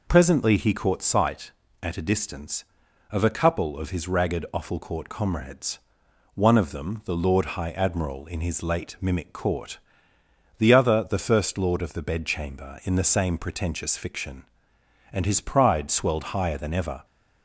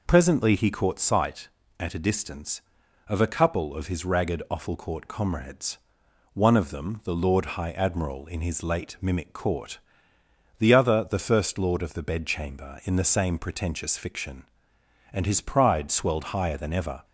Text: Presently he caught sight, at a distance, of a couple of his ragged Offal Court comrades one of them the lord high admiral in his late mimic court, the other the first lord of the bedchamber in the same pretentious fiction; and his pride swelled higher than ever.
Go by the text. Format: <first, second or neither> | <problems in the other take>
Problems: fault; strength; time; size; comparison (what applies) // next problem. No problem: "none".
neither | pauses between "comrades" and "one"; noticeable; the same in both